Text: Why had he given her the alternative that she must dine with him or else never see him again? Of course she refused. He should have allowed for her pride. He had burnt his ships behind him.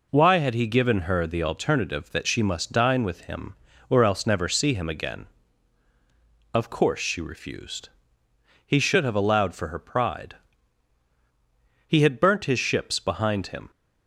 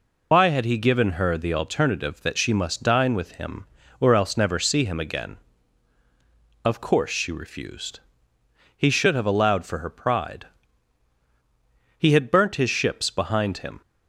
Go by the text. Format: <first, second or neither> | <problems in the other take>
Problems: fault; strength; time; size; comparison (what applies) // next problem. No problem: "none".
first | loses the start of "Why"; at 0.3 s; 105 ms